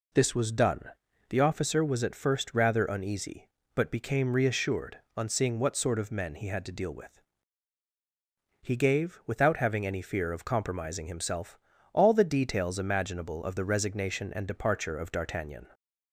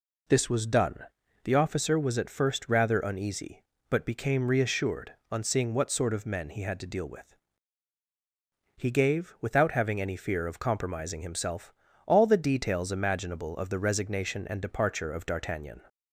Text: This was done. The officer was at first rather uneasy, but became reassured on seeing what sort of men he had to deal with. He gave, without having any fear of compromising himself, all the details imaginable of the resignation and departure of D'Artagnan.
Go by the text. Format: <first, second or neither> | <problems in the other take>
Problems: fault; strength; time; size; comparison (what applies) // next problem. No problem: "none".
neither | none